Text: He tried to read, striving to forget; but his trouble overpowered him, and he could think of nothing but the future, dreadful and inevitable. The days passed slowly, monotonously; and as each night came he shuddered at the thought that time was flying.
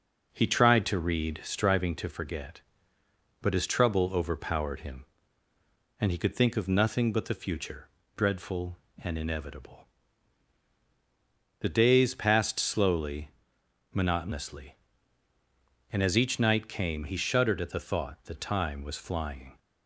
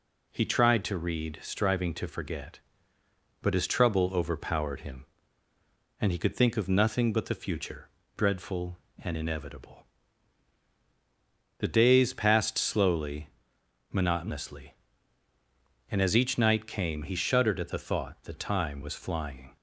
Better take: second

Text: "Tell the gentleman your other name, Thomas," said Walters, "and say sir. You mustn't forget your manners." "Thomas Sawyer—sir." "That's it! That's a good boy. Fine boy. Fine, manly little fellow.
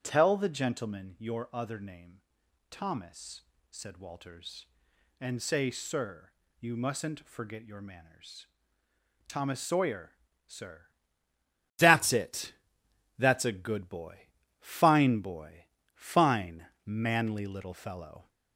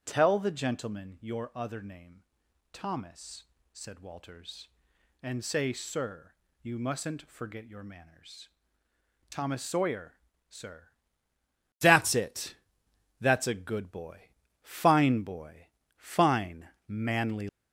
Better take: first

